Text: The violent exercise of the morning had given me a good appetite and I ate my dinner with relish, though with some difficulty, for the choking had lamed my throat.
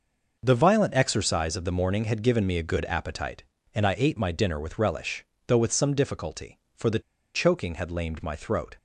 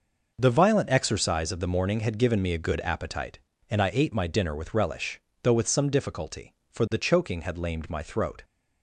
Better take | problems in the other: second | pauses between "the" and "choking"; slight; at 6.9 s; 0.34 s long

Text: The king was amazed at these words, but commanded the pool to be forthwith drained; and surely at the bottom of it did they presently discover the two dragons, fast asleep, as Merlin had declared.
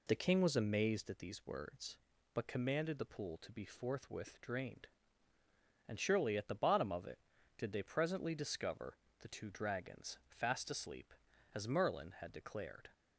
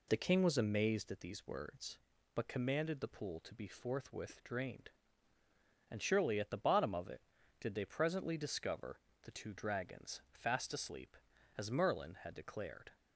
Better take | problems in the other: neither | pauses between "discover" and "the"; slight; the same in both

